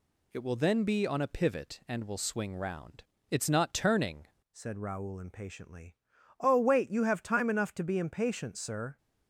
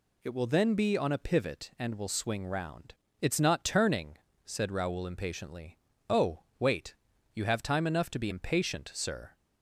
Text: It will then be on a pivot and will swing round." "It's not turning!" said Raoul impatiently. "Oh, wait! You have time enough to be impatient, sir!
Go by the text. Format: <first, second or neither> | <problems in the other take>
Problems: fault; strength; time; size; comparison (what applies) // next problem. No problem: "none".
second | changes voice at "said"; from 4.5 s on; 4.4 s long